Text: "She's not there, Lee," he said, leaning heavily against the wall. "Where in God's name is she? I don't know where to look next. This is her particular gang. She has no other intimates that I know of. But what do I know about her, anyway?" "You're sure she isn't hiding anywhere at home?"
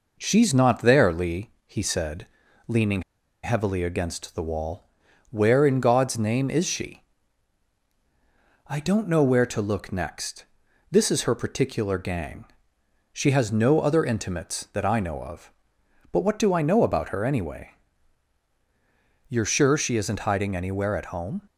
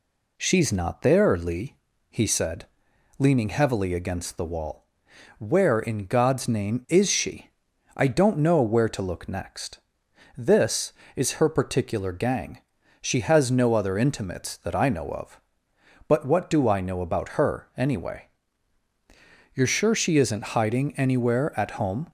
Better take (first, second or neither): second